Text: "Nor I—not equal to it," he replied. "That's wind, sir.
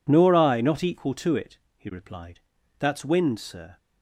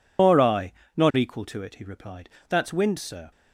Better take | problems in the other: first | loses the start of "Nor"; at 0.1 s; 150 ms

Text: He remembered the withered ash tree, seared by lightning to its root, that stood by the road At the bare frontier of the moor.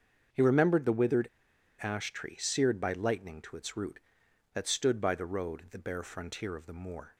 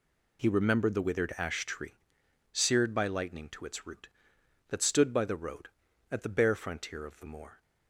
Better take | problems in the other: second | starts louder than the rest; until 1.8 s; 7 dB // pauses between "withered" and "ash"; noticeable; at 1.2 s; 0.55 s long

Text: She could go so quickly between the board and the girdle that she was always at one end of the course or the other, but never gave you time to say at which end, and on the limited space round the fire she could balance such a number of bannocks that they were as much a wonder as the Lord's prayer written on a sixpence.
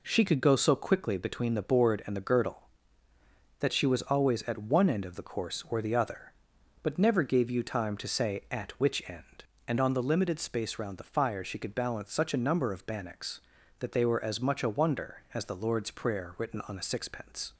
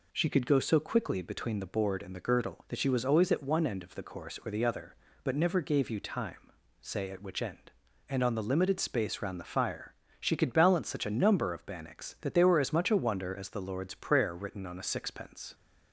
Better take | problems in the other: first | skips "to"; at 6.5 s // pauses between "fire" and "she"; slight; at 9.9 s; 0.26 s long

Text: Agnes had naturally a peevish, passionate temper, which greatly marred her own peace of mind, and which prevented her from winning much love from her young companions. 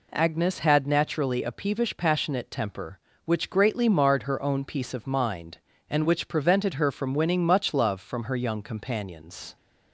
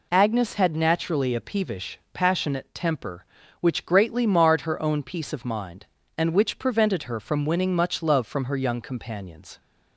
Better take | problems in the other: neither | none

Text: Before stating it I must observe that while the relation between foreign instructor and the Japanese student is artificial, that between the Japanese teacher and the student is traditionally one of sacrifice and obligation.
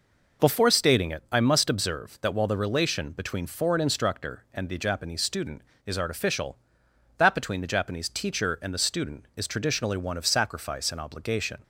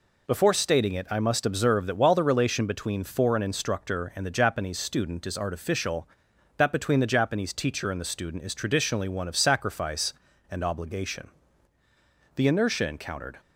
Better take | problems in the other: first | goes on to say "The inertia encountered"; noticeable; from 12.3 s on; 1.0 s long

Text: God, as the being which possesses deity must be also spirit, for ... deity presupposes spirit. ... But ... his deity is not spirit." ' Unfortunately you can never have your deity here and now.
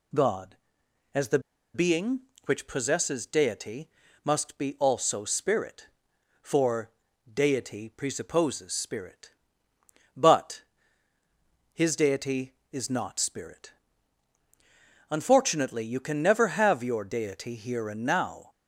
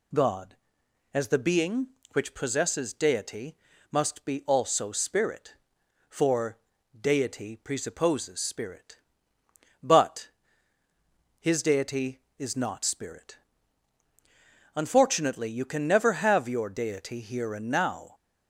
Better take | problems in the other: second | pauses between "the" and "being"; slight; at 1.3 s; 0.35 s long // pauses between "deity" and "must"; slight; at 3.8 s; 0.36 s long; slight in the second

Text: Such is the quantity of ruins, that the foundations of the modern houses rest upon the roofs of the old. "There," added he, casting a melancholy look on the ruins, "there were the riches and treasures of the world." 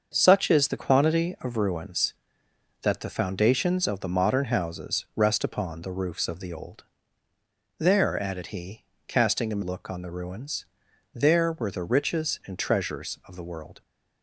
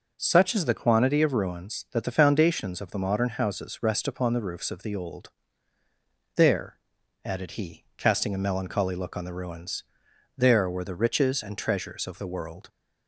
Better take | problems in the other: second | starts louder than the rest; until 1.1 s; 6.5 dB // skips "melancholy"; at 9.6 s

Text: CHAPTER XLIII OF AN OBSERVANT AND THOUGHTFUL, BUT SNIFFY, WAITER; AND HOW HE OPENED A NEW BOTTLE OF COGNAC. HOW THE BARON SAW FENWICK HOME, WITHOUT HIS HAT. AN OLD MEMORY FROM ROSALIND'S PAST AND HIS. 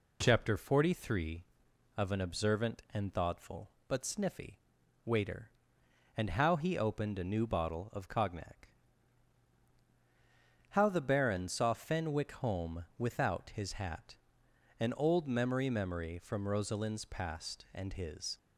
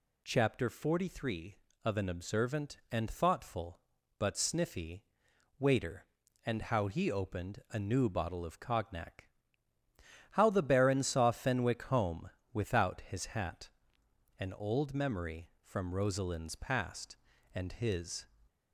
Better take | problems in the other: second | says "MEMORY" twice; at 15.7 s

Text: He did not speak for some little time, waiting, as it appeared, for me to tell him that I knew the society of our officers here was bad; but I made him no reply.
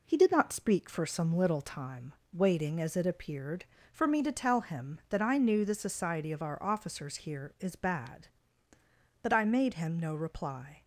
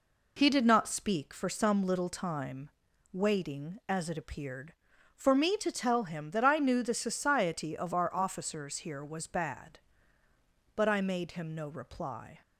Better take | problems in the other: second | says "is" for "was"; at 7.5 s

